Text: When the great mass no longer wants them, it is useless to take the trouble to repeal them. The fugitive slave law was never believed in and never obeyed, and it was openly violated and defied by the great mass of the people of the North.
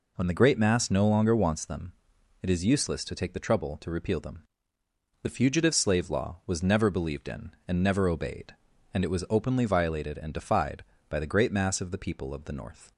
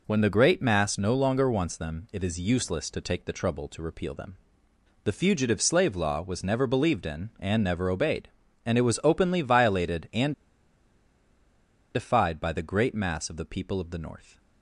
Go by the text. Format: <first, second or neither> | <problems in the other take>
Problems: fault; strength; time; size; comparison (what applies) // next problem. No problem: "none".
first | pauses between "and" and "defied"; strong; at 10.3 s; 1.6 s long